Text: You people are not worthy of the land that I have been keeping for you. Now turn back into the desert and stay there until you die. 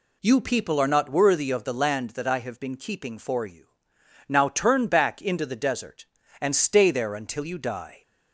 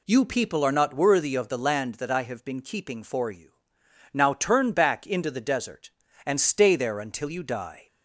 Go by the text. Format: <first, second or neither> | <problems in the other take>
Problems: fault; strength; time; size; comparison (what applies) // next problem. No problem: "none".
neither | none